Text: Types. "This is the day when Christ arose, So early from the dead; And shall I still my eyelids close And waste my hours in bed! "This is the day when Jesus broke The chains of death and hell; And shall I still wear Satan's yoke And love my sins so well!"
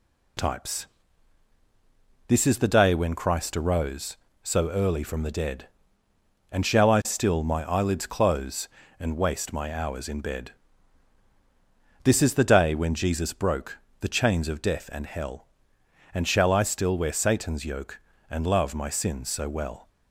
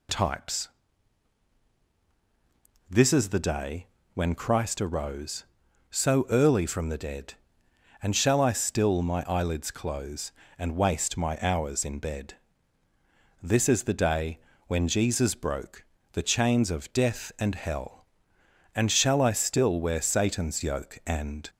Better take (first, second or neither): first